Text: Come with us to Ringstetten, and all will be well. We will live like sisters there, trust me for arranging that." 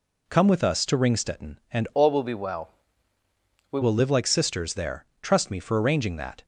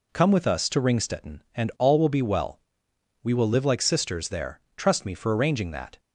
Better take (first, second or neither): second